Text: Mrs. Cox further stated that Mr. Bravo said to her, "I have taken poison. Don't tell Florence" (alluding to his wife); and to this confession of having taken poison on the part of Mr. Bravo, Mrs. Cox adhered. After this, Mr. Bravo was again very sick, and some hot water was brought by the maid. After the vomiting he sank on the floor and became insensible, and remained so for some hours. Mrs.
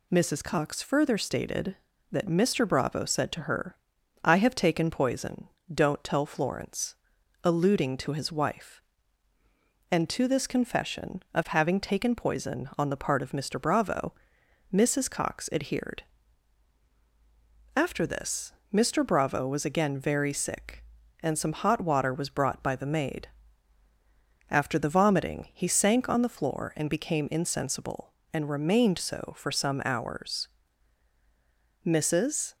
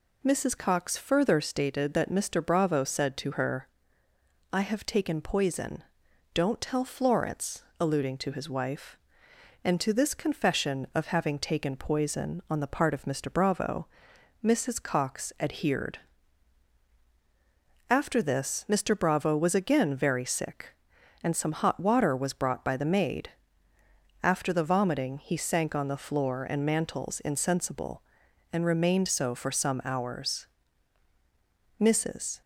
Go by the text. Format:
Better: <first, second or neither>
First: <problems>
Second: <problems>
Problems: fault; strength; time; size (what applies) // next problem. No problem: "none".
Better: first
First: none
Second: says "mantels" for "became"; at 26.6 s